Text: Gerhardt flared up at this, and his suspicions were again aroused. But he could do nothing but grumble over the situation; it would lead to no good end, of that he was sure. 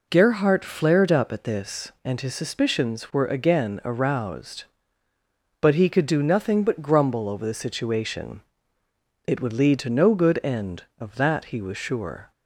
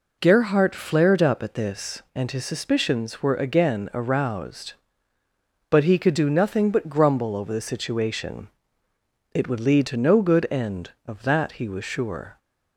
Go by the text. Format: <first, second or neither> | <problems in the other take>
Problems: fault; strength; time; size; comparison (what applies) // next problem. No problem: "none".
neither | none